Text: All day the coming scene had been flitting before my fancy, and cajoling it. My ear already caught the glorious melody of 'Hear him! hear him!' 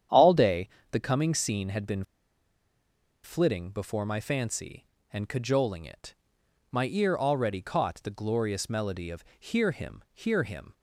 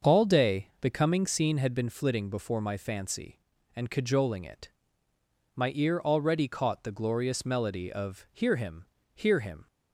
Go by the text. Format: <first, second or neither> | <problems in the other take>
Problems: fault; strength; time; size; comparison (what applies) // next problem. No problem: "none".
second | starts louder than the rest; strong; until 1.3 s; 9 dB; also in the second // pauses between "day" and "the"; slight; at 0.6 s; 0.22 s long // pauses between "been" and "flitting"; at 2.0 s; 1.2 s long // pauses between "of" and "Hear"; slight; at 9.2 s; 0.16 s long